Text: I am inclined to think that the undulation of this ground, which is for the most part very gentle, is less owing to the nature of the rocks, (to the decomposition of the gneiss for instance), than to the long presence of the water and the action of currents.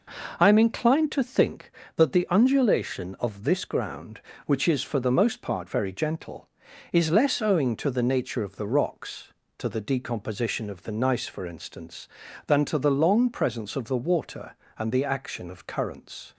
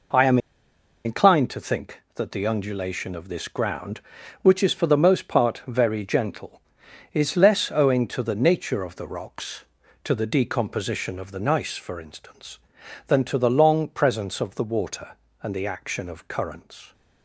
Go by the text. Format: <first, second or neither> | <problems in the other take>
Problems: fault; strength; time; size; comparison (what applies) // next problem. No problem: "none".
first | pauses between "am" and "inclined"; noticeable; at 0.3 s; 0.67 s long